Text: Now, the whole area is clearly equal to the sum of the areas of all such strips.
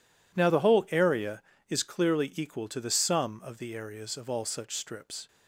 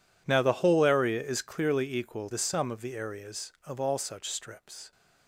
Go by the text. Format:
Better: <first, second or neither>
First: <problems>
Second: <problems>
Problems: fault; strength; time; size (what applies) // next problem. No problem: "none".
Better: first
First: none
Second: skips "to"; at 2.3 s